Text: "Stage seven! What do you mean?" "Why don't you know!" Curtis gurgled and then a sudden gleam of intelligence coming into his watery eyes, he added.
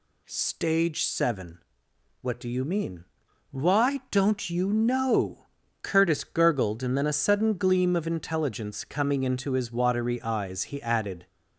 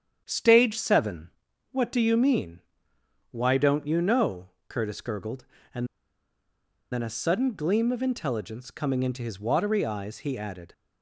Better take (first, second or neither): first